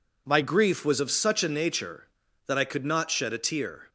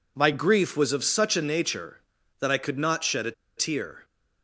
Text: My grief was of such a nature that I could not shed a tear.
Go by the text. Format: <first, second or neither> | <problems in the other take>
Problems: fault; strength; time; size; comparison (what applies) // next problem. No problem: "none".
first | pauses between "a" and "tear"; slight; at 3.3 s; 0.25 s long